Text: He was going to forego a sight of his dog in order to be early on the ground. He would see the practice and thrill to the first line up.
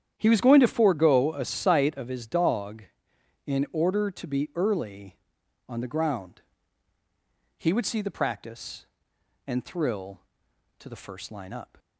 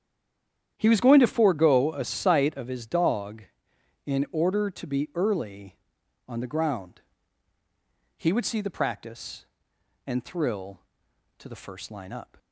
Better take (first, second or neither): first